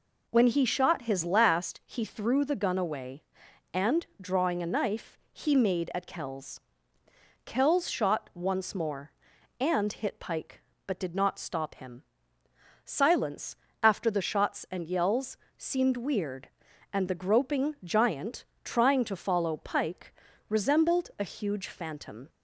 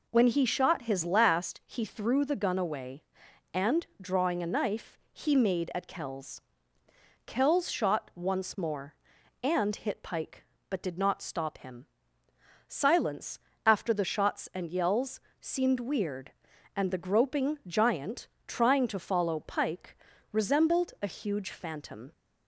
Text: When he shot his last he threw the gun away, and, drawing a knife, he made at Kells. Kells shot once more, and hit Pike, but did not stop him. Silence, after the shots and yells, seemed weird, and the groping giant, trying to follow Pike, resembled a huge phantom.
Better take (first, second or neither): neither